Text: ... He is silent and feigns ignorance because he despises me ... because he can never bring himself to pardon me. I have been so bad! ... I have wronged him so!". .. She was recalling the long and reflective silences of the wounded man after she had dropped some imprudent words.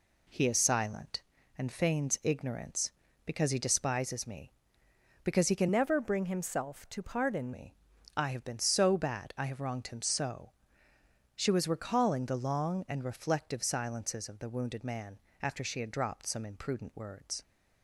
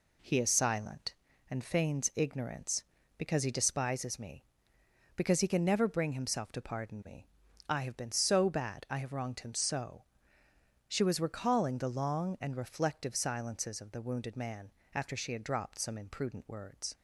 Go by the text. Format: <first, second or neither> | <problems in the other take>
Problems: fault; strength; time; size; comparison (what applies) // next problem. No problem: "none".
second | changes voice from "never" to "pardon"; from 5.7 to 7.5 s; 1.8 s long // pauses between "man" and "after"; slight; at 15.1 s; 0.24 s long; slight in the second